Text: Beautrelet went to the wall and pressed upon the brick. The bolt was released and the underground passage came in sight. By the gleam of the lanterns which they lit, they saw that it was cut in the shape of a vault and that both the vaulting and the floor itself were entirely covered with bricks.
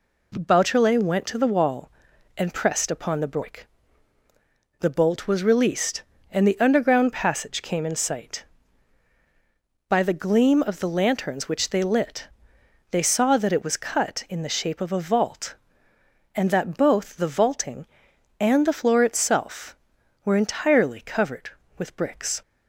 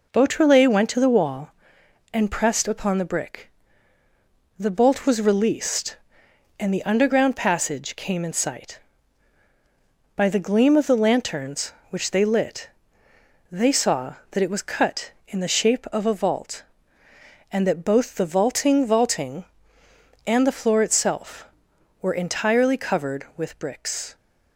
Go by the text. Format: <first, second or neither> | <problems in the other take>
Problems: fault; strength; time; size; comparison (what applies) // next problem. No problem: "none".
first | says "vaulting" twice; at 18.8 s